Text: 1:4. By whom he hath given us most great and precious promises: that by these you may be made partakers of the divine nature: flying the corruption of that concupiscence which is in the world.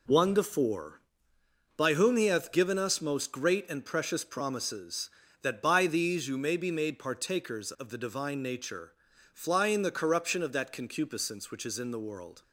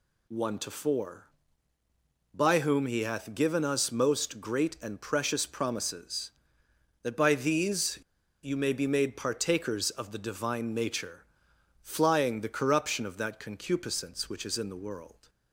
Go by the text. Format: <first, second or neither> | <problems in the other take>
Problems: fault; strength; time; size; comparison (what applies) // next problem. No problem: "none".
first | pauses between "these" and "you"; at 7.9 s; 0.45 s long